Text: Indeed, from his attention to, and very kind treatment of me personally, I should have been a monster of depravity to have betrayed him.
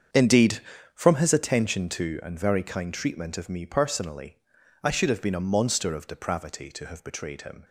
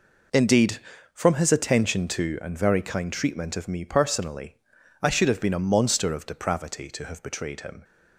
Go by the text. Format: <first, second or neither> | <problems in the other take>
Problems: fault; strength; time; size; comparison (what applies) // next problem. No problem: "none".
second | starts louder than the rest; strong; until 1.5 s; 7.5 dB